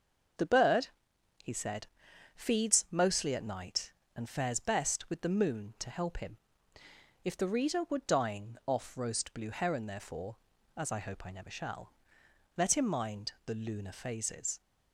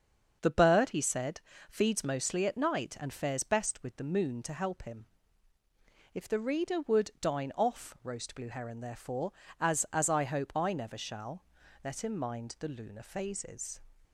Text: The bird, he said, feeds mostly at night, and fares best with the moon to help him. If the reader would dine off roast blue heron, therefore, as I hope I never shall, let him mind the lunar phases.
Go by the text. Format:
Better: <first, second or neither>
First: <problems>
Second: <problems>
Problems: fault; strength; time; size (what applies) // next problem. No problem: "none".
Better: first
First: starts louder than the rest; until 2.4 s; 6.5 dB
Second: starts louder than the rest; until 1.4 s; 6.5 dB // says "as" twice; at 9.9 s